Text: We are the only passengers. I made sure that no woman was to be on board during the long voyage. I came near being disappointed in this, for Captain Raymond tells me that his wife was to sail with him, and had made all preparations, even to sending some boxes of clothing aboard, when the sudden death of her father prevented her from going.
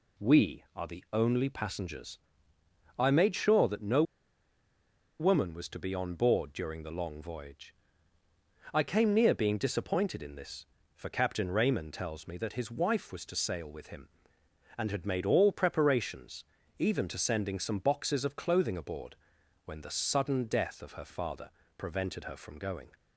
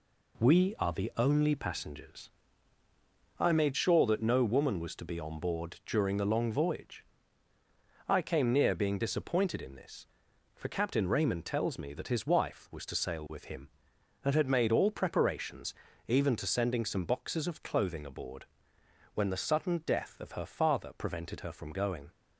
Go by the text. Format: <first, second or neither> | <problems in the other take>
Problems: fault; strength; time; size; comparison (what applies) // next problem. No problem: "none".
second | pauses between "no" and "woman"; at 4.0 s; 1.1 s long // pauses between "father" and "prevented"; slight; at 21.4 s; 0.28 s long